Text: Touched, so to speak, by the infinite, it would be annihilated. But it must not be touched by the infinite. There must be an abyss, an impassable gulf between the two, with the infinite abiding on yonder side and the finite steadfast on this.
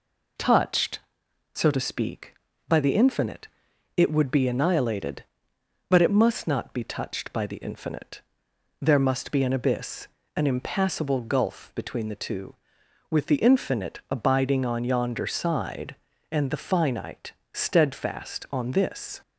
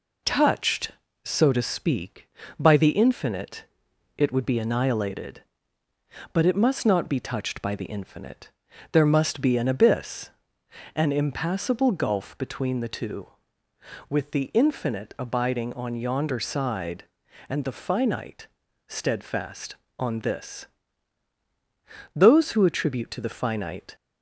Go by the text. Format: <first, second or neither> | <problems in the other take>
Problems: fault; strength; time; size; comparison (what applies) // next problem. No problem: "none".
first | pauses between "finite" and "steadfast"; at 18.4 s; 0.40 s long; slight in the first // goes on to say "Those who attribute to the finite"; strong; from 22.1 s on; 1.8 s long